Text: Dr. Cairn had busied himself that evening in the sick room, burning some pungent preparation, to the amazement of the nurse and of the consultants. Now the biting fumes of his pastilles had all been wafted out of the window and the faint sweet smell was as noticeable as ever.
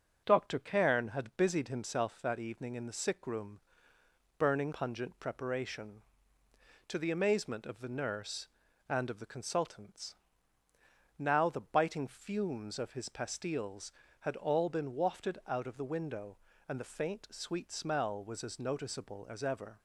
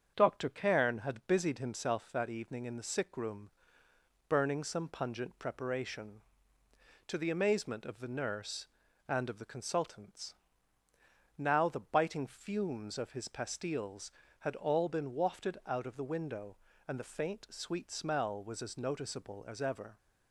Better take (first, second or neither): second